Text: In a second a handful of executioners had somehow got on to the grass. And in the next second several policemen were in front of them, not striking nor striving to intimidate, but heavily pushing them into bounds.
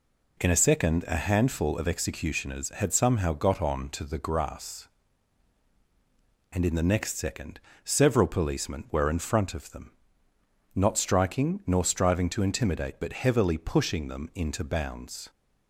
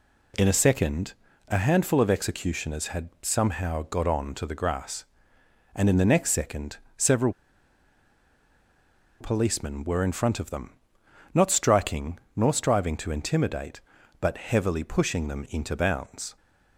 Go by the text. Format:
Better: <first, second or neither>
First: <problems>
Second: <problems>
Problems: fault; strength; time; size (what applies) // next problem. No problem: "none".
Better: first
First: pauses between "second" and "several"; slight; at 7.5 s; 0.28 s long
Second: pauses between "second" and "a"; slight; at 1.1 s; 0.34 s long // pauses between "second" and "several"; slight; at 6.7 s; 0.20 s long // pauses between "several" and "policemen"; strong; at 7.3 s; 1.8 s long // pauses between "striking" and "nor"; slight; at 12.2 s; 0.16 s long